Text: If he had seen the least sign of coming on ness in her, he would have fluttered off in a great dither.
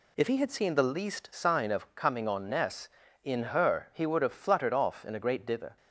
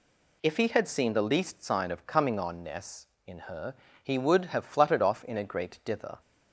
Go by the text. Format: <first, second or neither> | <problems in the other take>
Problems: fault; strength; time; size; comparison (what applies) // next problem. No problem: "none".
neither | none